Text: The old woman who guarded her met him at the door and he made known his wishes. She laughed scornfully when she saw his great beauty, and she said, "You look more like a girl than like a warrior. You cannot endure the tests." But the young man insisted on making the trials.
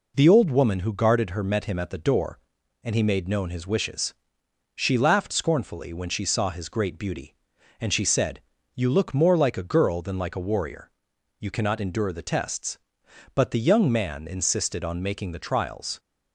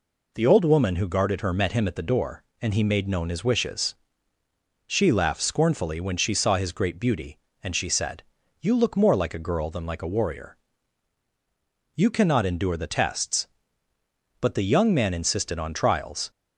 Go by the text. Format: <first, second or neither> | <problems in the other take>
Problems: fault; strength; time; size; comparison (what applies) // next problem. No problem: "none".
first | skips "making the"; at 15.7 s